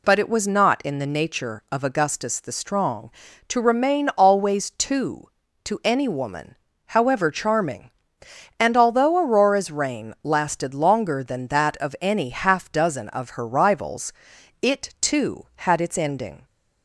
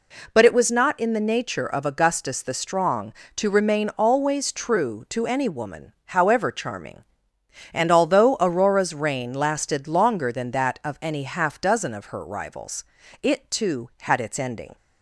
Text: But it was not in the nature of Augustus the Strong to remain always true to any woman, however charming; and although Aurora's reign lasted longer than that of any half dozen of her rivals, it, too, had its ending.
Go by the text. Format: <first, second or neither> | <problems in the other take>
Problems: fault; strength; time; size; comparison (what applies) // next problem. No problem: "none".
second | says "two" for "true"; at 4.6 s